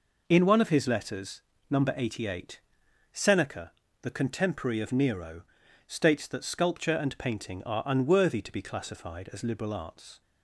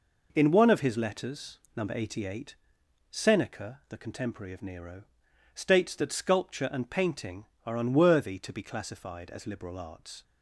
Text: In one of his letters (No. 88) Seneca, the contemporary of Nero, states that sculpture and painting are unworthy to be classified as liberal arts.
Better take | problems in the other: neither | none

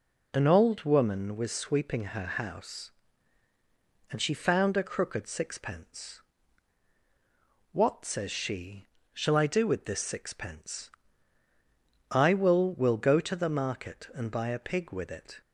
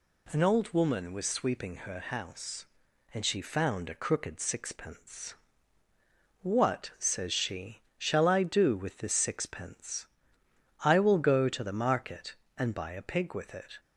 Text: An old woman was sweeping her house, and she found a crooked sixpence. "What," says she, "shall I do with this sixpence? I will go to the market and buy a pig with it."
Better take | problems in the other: second | says "will" twice; at 12.7 s

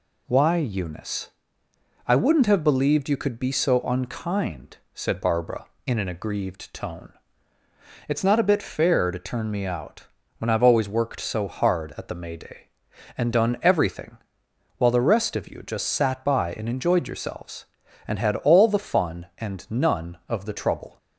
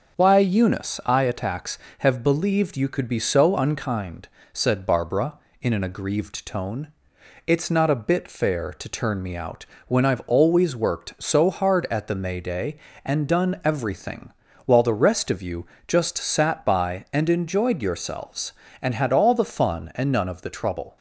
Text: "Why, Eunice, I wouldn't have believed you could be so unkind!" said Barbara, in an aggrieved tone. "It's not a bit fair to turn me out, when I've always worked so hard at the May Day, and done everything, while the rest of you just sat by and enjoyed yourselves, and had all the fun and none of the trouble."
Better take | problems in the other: first | starts louder than the rest; until 1.2 s; 6.5 dB // says "attacks" for "wouldn't"; at 1.2 s // pauses between "you" and "just"; slight; at 15.6 s; 0.22 s long

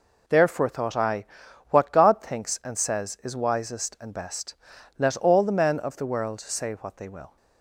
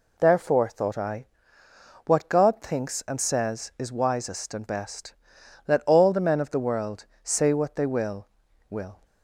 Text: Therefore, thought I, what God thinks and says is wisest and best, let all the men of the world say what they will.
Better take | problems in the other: first | pauses between "world" and "say"; slight; at 7.0 s; 0.18 s long // says "will" twice; at 8.6 s

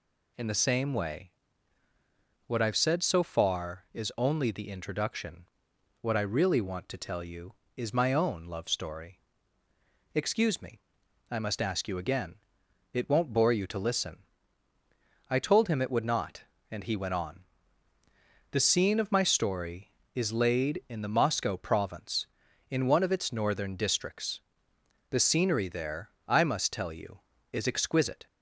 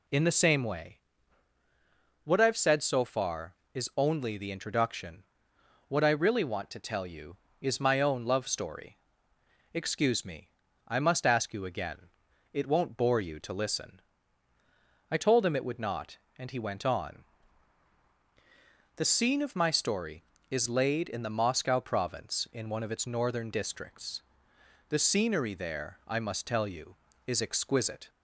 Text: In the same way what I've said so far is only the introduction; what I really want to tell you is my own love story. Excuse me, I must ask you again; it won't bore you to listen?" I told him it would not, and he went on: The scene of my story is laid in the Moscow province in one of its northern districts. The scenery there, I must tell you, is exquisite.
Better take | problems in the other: neither | pauses between "way" and "what"; the same in both

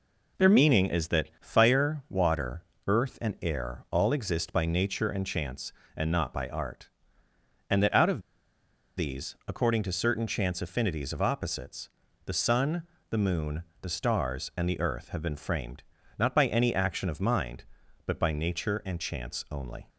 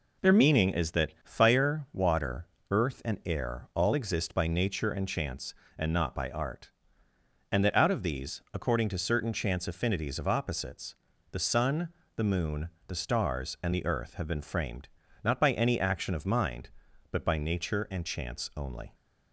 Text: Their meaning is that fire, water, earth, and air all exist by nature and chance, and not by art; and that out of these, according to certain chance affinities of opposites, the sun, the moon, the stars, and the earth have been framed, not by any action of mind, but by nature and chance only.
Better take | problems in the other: second | pauses between "of" and "these"; noticeable; at 8.1 s; 0.78 s long

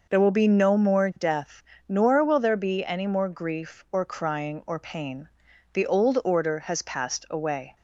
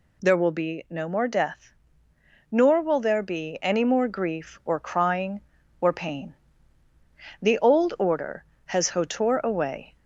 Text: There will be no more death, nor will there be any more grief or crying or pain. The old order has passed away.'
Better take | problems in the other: first | says "hotor" for "passed"; at 8.8 s

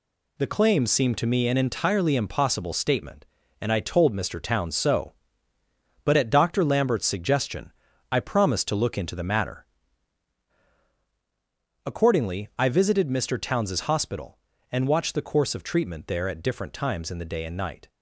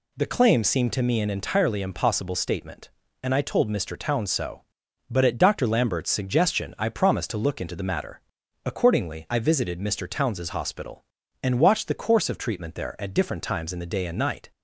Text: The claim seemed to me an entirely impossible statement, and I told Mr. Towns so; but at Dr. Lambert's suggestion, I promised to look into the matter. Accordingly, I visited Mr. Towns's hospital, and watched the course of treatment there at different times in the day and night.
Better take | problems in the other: neither | none

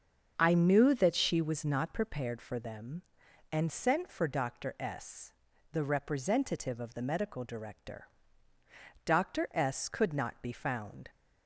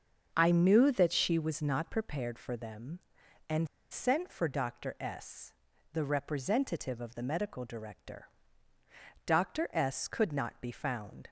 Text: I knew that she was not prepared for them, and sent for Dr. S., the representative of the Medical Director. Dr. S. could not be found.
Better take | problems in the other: first | starts louder than the rest; until 1.3 s; 6.5 dB; also in the first // pauses between "and" and "sent"; slight; at 3.6 s; 0.23 s long

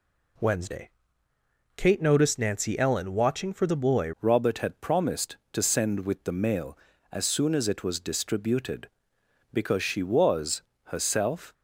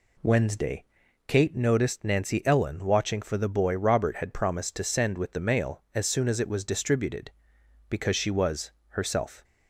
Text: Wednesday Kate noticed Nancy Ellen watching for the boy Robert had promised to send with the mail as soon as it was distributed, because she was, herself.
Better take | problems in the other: second | pauses between "Wednesday" and "Kate"; noticeable; at 0.9 s; 0.86 s long; also in the second // changes voice at "Robert"; from 4.2 s on; 7.3 s long

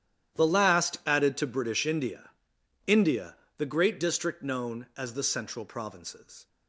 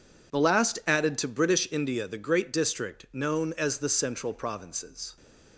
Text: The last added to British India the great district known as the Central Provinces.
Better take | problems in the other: second | starts louder than the rest; strong; until 1.4 s; 11.5 dB // says "India" twice; at 2.8 s

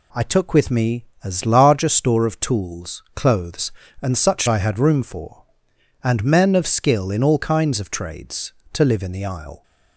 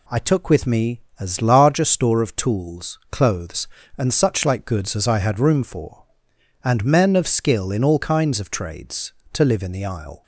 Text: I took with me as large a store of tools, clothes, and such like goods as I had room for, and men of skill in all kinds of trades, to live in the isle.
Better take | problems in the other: second | skips "like goods as"; at 4.4 s

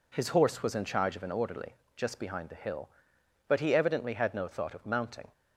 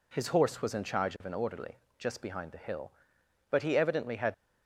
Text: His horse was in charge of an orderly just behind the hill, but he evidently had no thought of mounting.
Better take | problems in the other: first | pauses between "orderly" and "just"; slight; at 1.7 s; 0.22 s long; slight in the first // stops before "no thought of mounting"; at 4.3 s

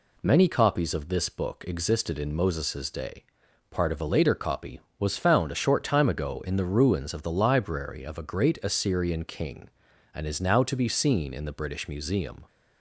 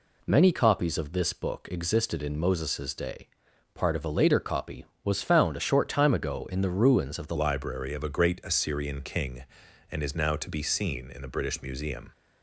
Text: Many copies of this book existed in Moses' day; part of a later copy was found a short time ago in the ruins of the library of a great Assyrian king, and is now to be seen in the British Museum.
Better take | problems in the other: first | changes voice at "library"; from 7.3 s on; 4.8 s long

